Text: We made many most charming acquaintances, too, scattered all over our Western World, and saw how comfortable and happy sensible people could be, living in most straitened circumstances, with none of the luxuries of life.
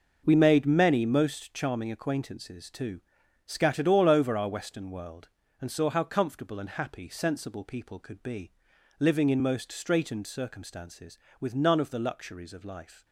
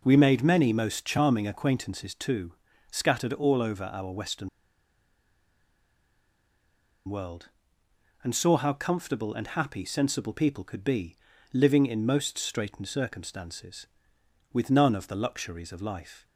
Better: first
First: none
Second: pauses between "Western" and "World"; strong; at 4.4 s; 2.5 s long

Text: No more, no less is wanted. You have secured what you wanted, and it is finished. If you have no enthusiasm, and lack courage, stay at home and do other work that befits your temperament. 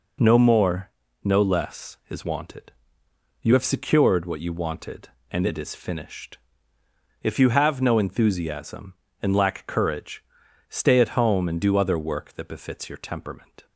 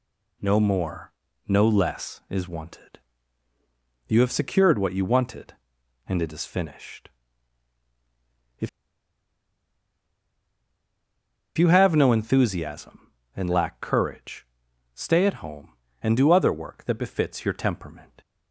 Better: first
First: none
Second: pauses between "If" and "you"; strong; at 8.6 s; 2.8 s long

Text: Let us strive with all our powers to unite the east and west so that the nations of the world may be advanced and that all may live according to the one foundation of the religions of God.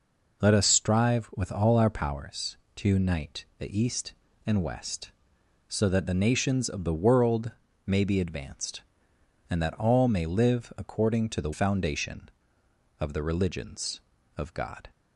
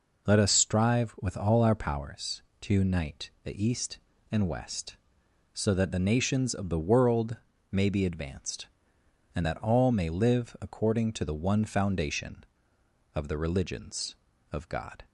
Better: second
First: pauses between "world" and "may"; slight; at 7.5 s; 0.34 s long // skips "one"; at 11.5 s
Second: pauses between "world" and "may"; slight; at 7.3 s; 0.34 s long

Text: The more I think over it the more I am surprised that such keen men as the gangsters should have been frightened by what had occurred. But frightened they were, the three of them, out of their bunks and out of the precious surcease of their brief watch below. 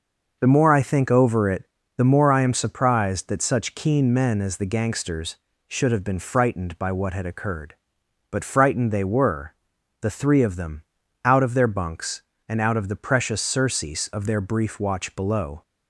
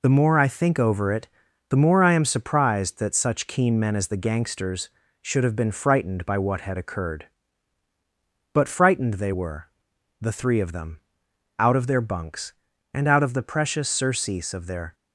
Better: first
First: pauses between "it" and "the"; slight; at 1.6 s; 0.32 s long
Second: pauses between "it" and "the"; at 1.2 s; 0.42 s long // stops before "brief watch below"; at 14.9 s

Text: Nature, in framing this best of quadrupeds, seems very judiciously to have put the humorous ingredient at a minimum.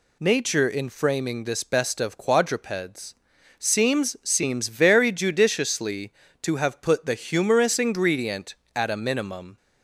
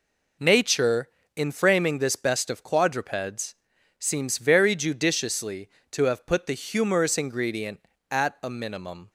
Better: second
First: says "seems" twice; at 4.2 s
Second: none

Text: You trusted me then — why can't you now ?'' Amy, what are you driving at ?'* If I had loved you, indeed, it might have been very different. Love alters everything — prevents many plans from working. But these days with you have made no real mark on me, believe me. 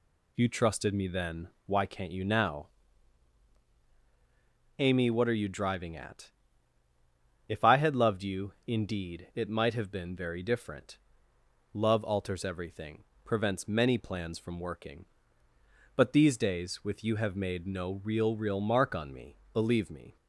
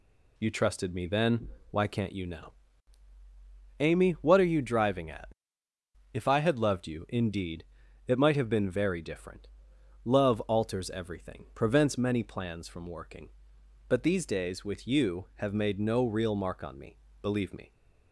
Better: second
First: says "real" twice; at 18.3 s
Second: none

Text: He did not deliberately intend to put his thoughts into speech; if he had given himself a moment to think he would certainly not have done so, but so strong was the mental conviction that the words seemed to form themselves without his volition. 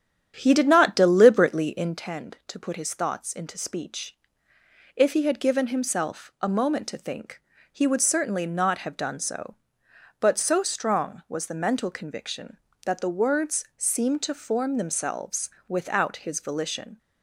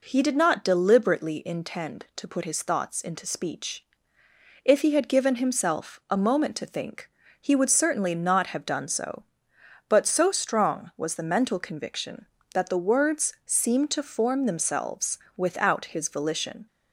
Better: second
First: starts louder than the rest; strong; until 2.0 s; 9 dB // pauses between "think" and "he"; slight; at 7.3 s; 0.32 s long // pauses between "themselves" and "without"; slight; at 15.4 s; 0.18 s long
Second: pauses between "think" and "he"; slight; at 7.0 s; 0.32 s long // pauses between "themselves" and "without"; slight; at 15.1 s; 0.18 s long

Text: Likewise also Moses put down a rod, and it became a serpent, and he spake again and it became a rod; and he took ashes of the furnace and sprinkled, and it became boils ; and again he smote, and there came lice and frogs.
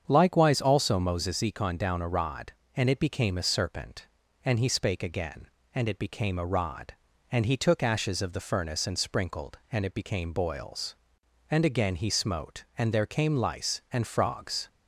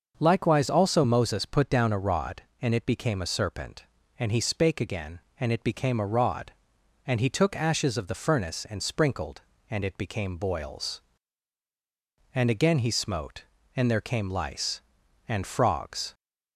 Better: second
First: starts louder than the rest; strong; until 1.0 s; 7.5 dB // says "econ" for "put"; at 1.3 s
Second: starts louder than the rest; until 1.2 s; 6.5 dB

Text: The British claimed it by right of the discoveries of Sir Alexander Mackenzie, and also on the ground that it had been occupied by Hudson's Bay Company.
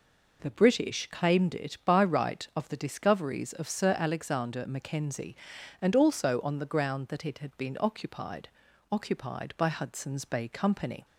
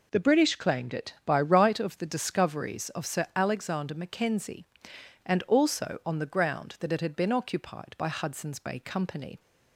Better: second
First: says "occupied" twice; at 8.9 s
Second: none

